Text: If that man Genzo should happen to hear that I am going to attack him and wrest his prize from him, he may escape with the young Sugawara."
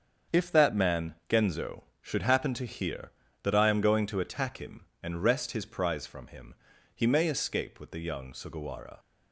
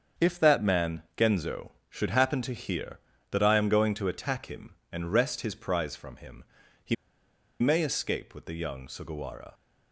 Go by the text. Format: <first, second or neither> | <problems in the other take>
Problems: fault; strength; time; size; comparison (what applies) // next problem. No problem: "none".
first | starts louder than the rest; strong; until 1.3 s; 7.5 dB; strong in the first // pauses between "man" and "Genzo"; slight; at 1.0 s; 0.16 s long; slight in the first // pauses between "he" and "may"; noticeable; at 6.9 s; 0.66 s long